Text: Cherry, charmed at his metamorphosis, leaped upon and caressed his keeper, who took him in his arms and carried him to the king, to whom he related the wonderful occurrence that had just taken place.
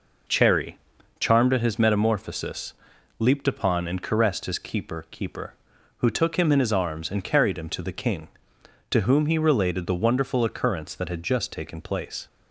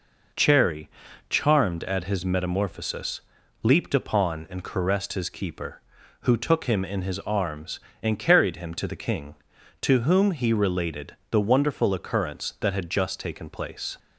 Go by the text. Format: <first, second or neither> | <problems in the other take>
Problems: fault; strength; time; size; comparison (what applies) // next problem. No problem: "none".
second | says "keeper" twice; at 5.1 s